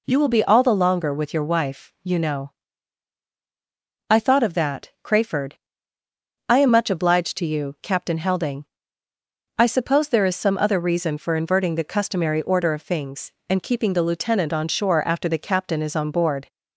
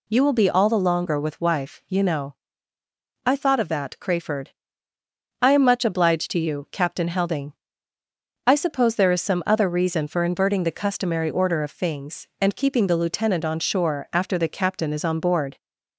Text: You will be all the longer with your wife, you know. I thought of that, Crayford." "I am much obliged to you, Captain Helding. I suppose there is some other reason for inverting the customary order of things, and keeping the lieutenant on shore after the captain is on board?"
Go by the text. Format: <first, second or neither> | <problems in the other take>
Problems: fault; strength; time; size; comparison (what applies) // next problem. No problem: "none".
first | skips "your"; at 1.4 s